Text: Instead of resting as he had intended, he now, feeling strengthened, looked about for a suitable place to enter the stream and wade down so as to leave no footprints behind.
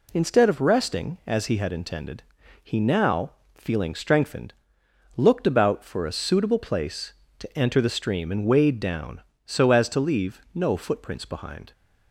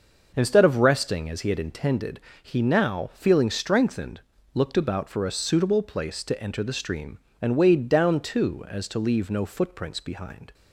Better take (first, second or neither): first